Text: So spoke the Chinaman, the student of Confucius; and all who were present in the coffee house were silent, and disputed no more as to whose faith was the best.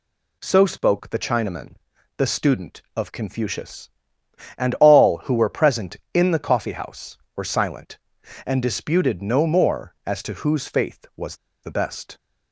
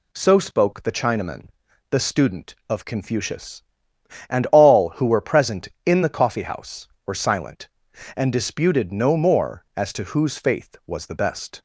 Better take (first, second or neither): second